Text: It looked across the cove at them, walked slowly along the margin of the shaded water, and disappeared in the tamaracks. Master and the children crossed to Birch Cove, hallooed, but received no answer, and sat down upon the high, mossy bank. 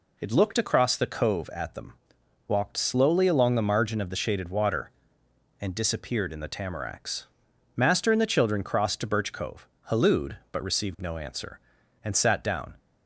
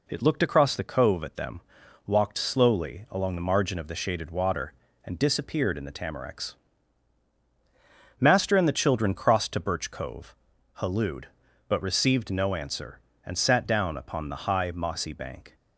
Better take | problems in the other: second | stops before "upon the high mossy bank"; at 12.7 s

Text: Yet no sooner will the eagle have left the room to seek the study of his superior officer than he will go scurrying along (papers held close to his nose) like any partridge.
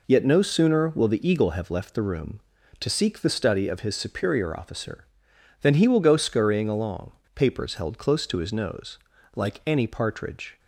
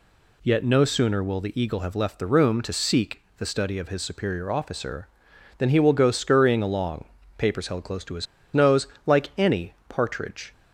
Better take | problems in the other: first | pauses between "seek" and "the"; slight; at 3.2 s; 0.16 s long // pauses between "his" and "nose"; slight; at 8.2 s; 0.28 s long // pauses between "any" and "partridge"; slight; at 9.7 s; 0.16 s long

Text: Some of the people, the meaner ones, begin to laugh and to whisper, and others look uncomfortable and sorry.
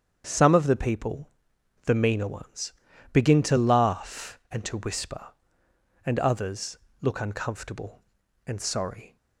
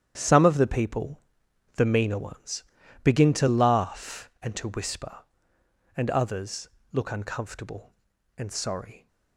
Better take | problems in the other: first | gets quieter; strong; throughout; 10 dB // starts louder than the rest; strong; until 1.1 s; 10 dB; strong in the first // pauses between "others" and "look"; slight; at 6.6 s; 0.24 s long; slight in the first

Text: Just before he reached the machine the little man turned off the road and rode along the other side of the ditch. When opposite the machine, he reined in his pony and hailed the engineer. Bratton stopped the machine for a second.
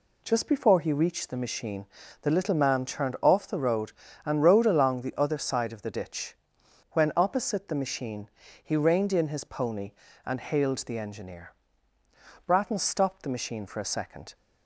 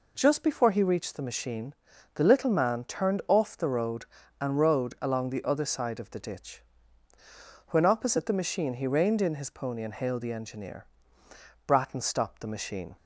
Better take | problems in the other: first | pauses between "machine" and "the"; at 1.7 s; 0.40 s long; slight in the first // stops before "for a second"; at 12.9 s

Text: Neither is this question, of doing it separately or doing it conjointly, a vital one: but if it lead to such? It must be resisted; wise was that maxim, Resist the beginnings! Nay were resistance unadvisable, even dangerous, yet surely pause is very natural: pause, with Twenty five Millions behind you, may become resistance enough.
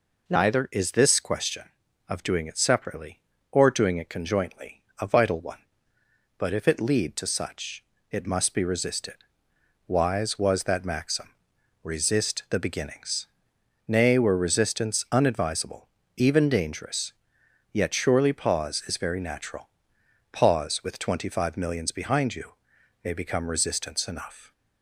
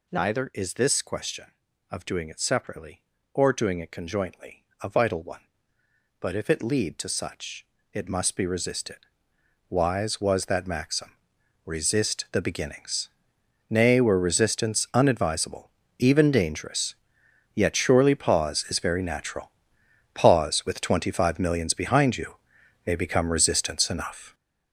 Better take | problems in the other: first | gets louder; strong; throughout; 8.5 dB

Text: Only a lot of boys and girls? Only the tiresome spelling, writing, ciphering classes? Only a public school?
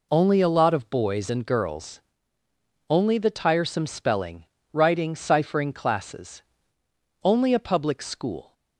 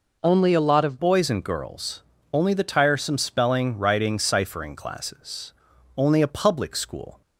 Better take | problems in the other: first | changes voice at "boys"; from 0.9 s on; 6.3 s long

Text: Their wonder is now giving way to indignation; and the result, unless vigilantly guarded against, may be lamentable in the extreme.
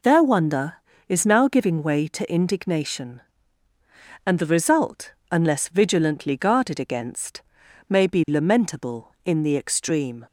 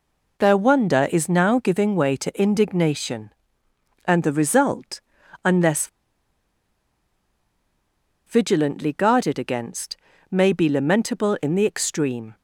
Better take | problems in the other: first | pauses between "unless" and "vigilantly"; strong; at 5.8 s; 2.3 s long

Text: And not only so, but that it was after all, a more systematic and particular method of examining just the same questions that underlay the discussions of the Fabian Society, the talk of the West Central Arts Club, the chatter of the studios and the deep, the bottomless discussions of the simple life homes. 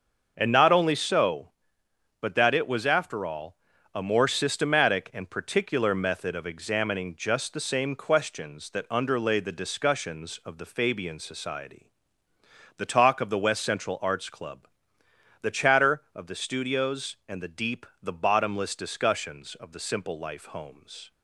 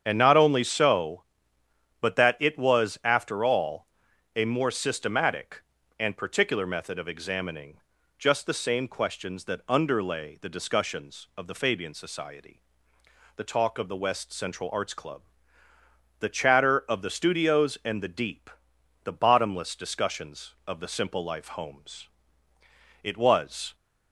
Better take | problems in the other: first | starts louder than the rest; strong; until 1.0 s; 8 dB; also in the first // pauses between "examining" and "just"; at 7.7 s; 0.40 s long // goes on to say "It was"; noticeable; from 23.0 s on; 0.72 s long

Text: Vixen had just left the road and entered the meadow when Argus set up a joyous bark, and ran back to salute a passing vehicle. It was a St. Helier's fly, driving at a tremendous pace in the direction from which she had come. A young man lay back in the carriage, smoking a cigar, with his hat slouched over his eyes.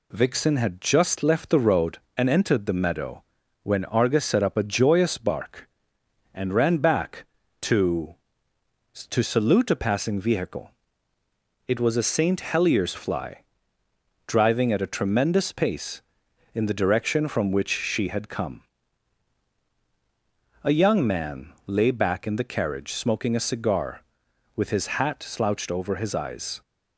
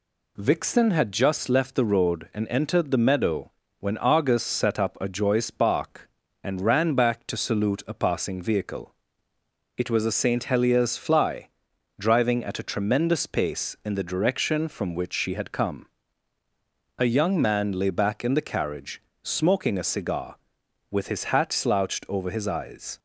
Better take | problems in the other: second | pauses between "meadow" and "when"; at 3.2 s; 0.40 s long; slight in the second // says "to" twice; at 9.0 s

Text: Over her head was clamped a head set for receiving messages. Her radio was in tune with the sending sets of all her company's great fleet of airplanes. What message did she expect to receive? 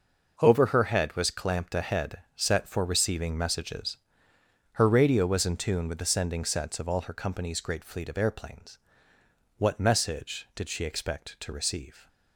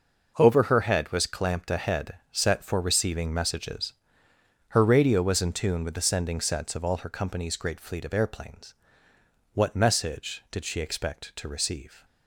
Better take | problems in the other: neither | pauses between "head" and "set"; slight; the same in both

